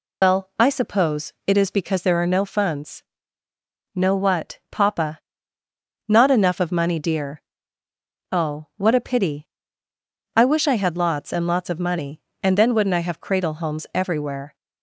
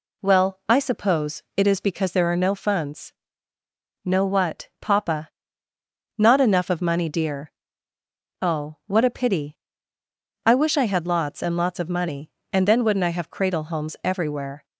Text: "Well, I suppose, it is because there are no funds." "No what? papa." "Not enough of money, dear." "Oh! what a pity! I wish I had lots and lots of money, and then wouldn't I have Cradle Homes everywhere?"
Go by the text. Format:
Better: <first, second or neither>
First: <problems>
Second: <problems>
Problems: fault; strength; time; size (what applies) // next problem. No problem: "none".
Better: second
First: loses the start of "Well"; at 0.2 s; 105 ms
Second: none